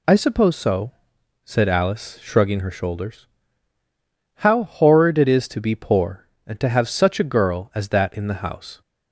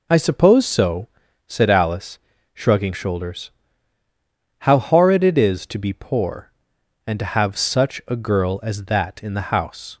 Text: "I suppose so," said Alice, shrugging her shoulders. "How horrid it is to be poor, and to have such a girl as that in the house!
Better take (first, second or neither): first